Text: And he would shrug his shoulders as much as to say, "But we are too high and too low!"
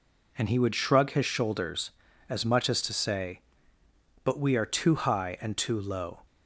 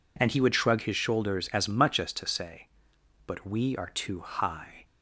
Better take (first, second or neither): first